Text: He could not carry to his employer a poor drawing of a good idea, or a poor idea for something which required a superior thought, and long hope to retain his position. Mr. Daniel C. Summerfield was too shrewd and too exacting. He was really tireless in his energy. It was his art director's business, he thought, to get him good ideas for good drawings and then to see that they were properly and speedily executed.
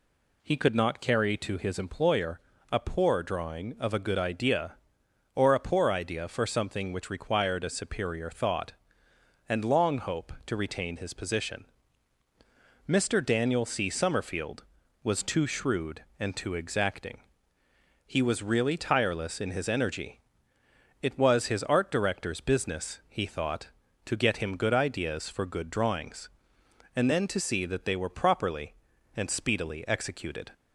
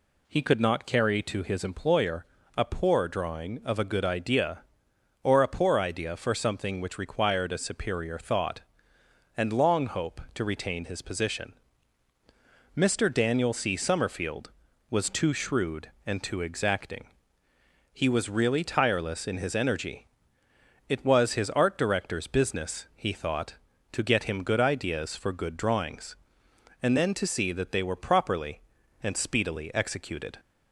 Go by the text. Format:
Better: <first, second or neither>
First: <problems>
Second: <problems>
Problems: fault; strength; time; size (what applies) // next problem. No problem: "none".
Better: neither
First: pauses between "employer" and "a"; slight; at 2.3 s; 0.32 s long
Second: pauses between "employer" and "a"; slight; at 2.2 s; 0.32 s long